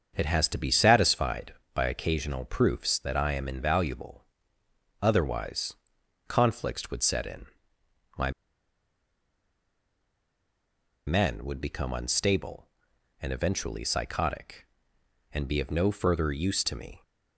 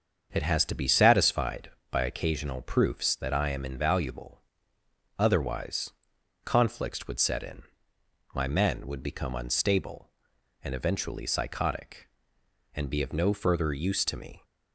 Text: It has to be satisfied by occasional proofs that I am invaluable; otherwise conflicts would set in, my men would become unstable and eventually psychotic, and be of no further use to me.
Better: second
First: starts louder than the rest; until 1.1 s; 7 dB // pauses between "otherwise" and "conflicts"; noticeable; at 5.7 s; 0.54 s long // pauses between "my" and "men"; strong; at 8.3 s; 2.7 s long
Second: starts louder than the rest; until 1.3 s; 7 dB // pauses between "otherwise" and "conflicts"; noticeable; at 5.9 s; 0.54 s long

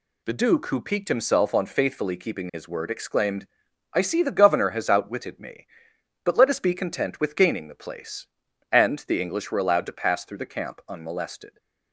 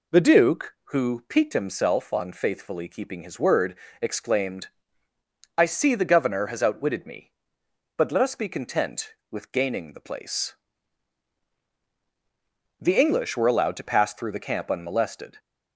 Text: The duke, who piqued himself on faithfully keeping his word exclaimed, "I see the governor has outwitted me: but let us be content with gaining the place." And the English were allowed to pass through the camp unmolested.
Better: first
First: none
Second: pauses between "word" and "exclaimed"; slight; at 3.7 s; 0.24 s long // skips "And"; at 11.6 s

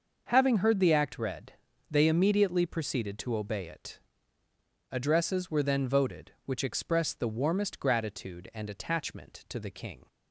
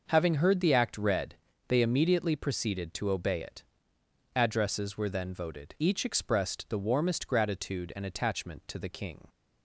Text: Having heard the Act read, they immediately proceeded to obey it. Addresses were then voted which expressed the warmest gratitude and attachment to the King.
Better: first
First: starts louder than the rest; until 1.3 s; 6 dB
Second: starts louder than the rest; noticeable; until 1.1 s; 6 dB // says "each" for "which"; at 5.8 s

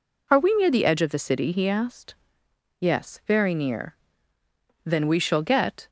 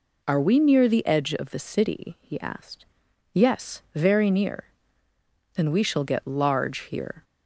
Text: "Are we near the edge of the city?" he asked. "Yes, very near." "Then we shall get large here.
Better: second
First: stops before "large here"; at 5.8 s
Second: none

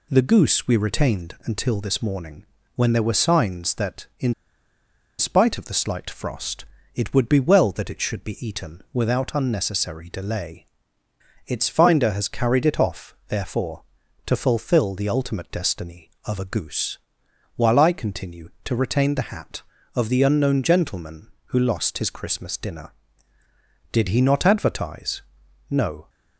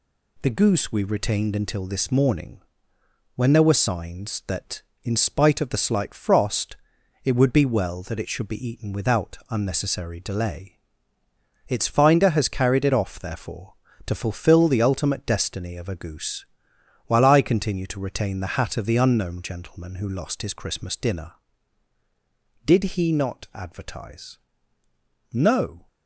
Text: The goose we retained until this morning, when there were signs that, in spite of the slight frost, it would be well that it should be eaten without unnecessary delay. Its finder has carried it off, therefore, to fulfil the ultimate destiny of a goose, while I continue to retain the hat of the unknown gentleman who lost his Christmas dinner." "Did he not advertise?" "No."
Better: second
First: pauses between "in" and "spite"; noticeable; at 4.3 s; 0.86 s long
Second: none

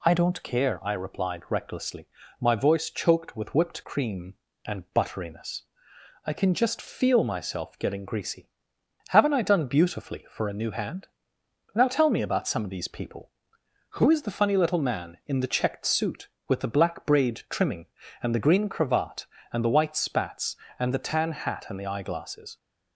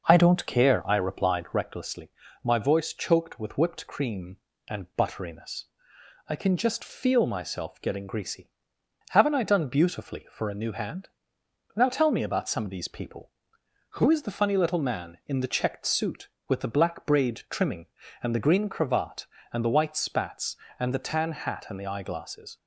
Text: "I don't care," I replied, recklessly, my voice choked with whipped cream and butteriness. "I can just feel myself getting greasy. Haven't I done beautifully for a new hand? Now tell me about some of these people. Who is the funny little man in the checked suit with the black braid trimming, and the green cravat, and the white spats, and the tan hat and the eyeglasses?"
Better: first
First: none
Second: starts louder than the rest; noticeable; until 1.6 s; 6 dB

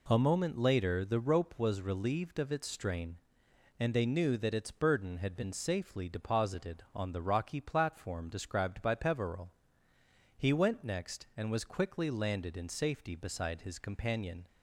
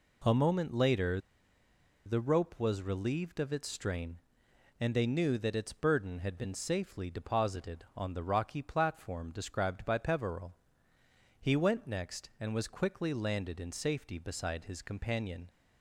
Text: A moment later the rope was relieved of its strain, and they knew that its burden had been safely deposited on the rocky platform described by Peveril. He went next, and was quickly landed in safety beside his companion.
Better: first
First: none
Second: pauses between "later" and "the"; noticeable; at 1.1 s; 0.87 s long

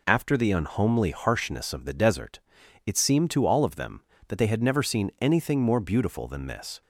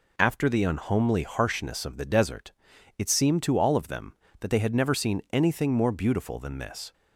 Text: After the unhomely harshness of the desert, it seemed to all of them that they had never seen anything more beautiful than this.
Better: neither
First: none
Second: none

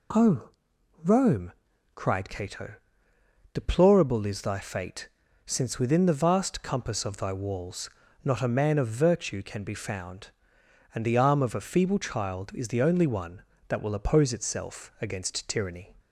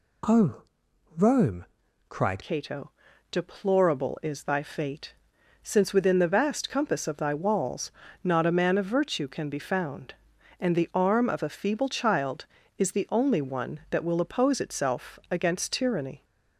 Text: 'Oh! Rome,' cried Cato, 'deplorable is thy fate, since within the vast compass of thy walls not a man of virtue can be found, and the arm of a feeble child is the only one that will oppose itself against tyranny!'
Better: first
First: pauses between "walls" and "not"; slight; at 7.8 s; 0.36 s long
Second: changes voice at "Cato"; from 2.4 s on; 13.8 s long // pauses between "walls" and "not"; slight; at 7.9 s; 0.32 s long

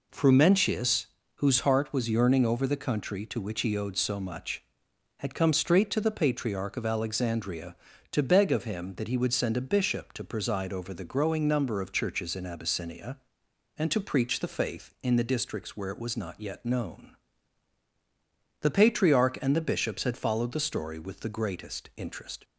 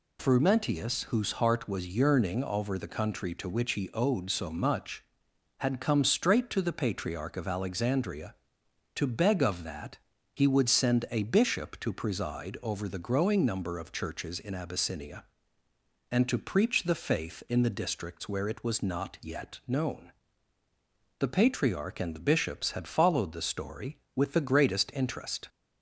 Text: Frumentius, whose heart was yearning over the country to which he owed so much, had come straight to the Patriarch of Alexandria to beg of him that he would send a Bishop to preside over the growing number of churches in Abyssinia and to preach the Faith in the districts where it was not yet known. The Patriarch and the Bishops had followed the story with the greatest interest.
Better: first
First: none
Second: skips "him"; at 9.6 s // pauses between "that" and "he"; at 9.9 s; 0.38 s long

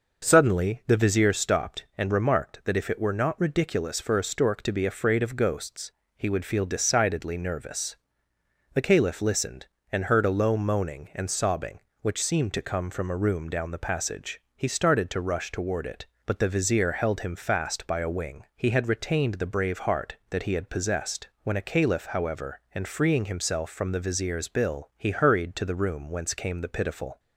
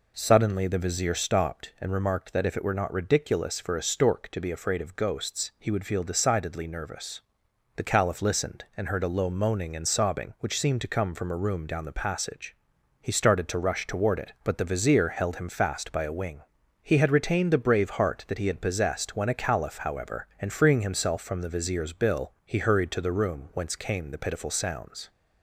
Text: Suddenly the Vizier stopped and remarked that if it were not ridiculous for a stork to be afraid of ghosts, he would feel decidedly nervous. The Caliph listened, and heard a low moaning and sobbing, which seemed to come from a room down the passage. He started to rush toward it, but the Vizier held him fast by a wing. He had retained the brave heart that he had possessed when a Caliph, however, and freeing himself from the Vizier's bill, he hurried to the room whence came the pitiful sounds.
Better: second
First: pauses between "possessed" and "when"; slight; at 21.2 s; 0.16 s long // stops before "sounds"; at 27.1 s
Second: none

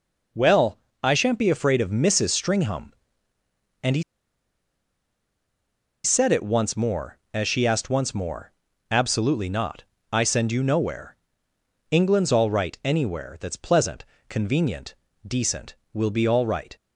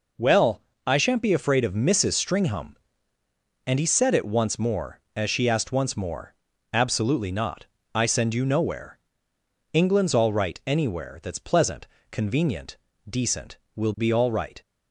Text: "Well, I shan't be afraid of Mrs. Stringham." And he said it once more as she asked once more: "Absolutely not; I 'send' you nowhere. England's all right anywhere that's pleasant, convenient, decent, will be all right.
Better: second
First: pauses between "he" and "said"; strong; at 4.0 s; 2.0 s long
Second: none

